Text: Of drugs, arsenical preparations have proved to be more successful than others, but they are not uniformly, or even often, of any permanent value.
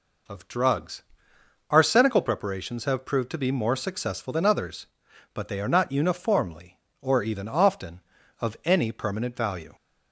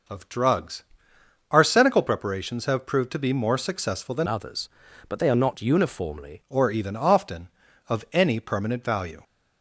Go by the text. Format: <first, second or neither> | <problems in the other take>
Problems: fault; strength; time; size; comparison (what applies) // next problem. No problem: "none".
first | changes voice from "others" to "uniformly"; from 4.2 to 6.4 s; 2.2 s long